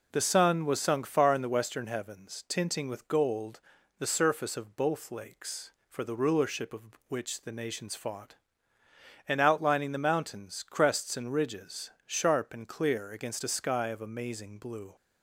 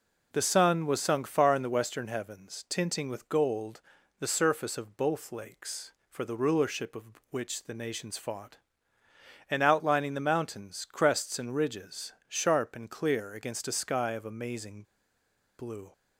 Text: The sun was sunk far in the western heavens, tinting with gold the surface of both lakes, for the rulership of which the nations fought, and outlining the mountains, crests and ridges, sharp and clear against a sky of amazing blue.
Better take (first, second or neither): first